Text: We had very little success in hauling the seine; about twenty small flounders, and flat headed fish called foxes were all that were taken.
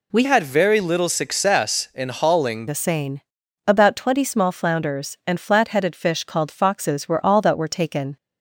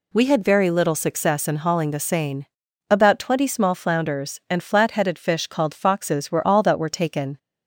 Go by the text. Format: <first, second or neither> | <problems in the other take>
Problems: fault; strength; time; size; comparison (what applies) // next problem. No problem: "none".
second | changes voice from "had" to "hauling"; from 0.2 to 2.6 s; 2.4 s long